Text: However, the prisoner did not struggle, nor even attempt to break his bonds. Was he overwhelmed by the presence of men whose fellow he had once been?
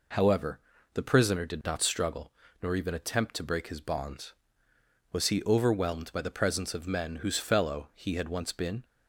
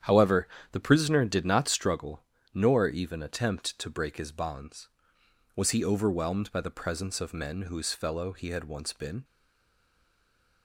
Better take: first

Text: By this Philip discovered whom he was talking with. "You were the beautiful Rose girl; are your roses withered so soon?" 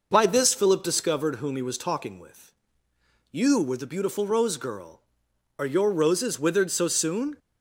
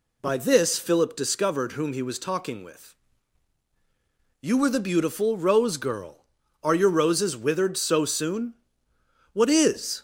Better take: first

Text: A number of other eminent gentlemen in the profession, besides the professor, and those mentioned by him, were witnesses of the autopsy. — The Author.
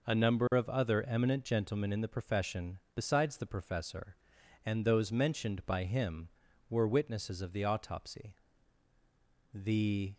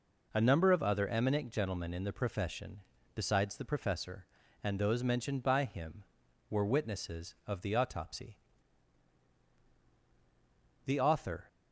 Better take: second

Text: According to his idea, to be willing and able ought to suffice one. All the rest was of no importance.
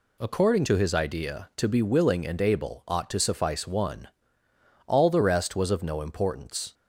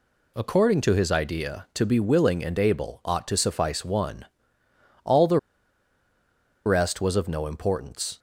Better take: first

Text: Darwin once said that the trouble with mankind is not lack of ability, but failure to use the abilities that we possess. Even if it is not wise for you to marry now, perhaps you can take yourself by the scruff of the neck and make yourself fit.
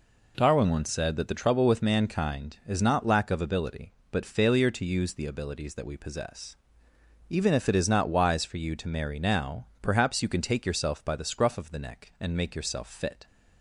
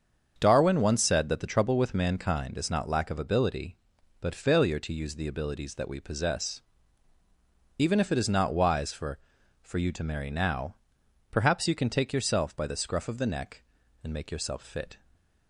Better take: first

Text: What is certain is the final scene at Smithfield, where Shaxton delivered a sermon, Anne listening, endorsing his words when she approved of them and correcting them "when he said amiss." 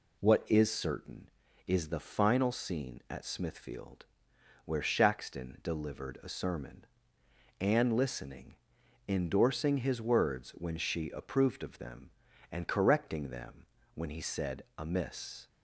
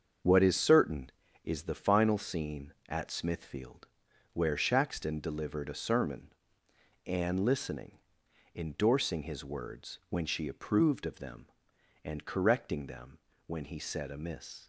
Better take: first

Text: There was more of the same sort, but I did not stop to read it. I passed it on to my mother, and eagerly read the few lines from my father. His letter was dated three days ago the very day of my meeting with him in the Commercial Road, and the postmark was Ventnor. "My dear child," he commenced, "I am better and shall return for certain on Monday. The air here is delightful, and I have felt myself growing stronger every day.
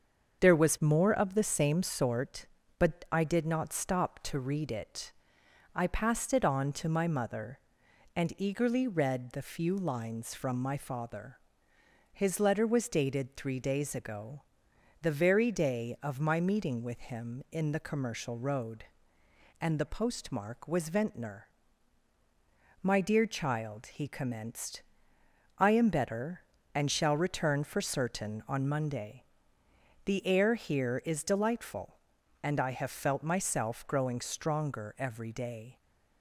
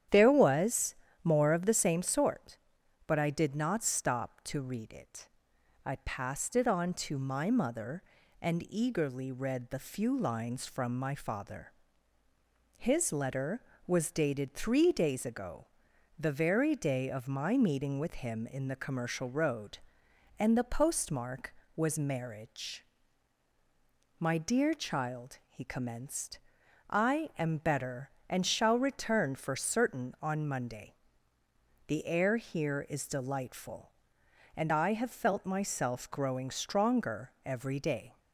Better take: first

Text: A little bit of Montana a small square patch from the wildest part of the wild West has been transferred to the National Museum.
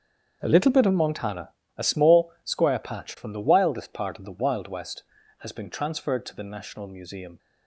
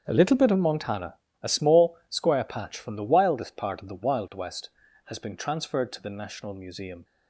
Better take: neither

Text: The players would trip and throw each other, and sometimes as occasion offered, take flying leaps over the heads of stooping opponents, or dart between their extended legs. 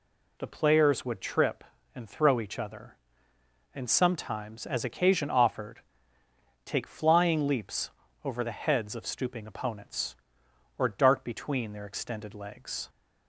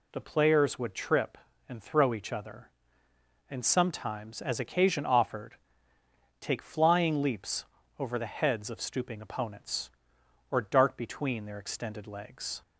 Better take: neither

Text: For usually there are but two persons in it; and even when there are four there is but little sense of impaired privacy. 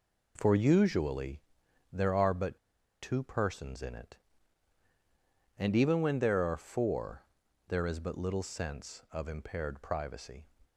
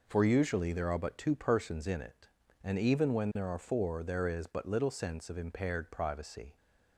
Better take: second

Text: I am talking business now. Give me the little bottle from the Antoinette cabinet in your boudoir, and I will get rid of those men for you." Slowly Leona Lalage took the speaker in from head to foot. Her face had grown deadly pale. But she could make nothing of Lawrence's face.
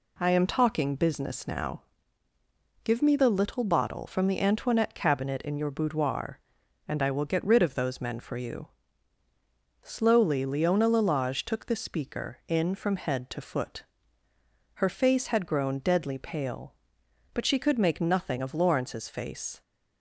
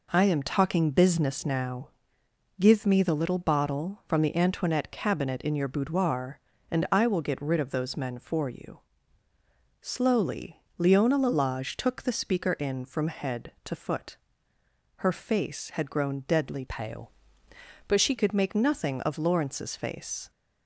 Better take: first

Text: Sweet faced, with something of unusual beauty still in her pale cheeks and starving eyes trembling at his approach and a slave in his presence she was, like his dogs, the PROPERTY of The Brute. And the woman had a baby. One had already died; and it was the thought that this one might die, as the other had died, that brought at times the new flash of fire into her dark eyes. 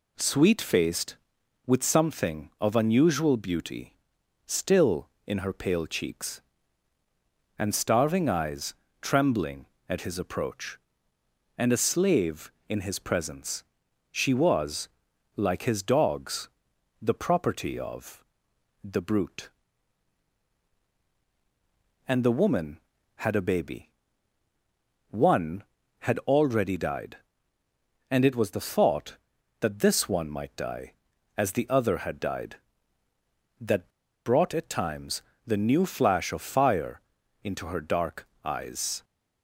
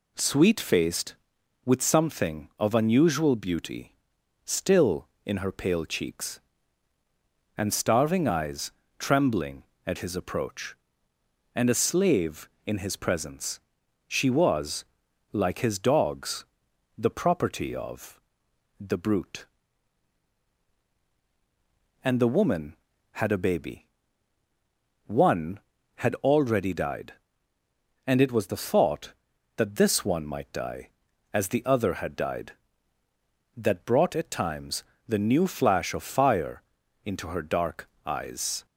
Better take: second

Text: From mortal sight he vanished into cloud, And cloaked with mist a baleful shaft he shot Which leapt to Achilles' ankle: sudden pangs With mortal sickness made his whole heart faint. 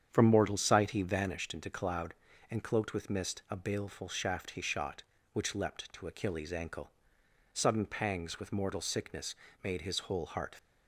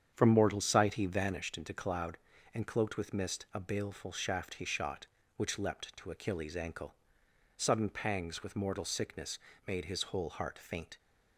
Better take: second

